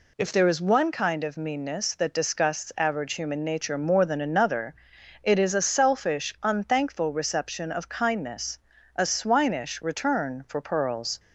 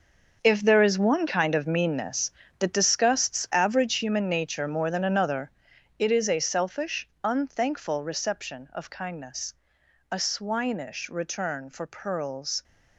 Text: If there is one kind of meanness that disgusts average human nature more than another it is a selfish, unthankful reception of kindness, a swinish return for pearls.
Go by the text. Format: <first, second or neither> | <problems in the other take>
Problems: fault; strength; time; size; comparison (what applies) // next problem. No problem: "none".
first | gets quieter; strong; throughout; 12 dB // pauses between "another" and "it"; noticeable; at 5.5 s; 0.48 s long; noticeable in the first